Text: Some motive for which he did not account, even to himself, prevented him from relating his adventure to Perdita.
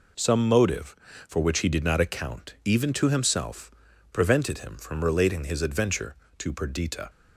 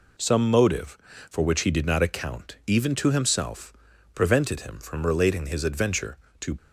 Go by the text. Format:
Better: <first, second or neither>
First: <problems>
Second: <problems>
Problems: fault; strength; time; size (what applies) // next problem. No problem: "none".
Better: first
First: none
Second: stops before "Perdita"; at 6.5 s